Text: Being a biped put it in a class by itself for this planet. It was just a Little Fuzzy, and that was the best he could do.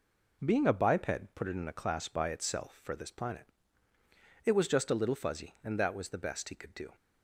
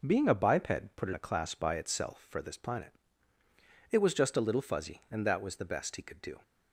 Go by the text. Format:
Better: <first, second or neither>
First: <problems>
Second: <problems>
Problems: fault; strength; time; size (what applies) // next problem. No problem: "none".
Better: first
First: none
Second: skips "in"; at 1.1 s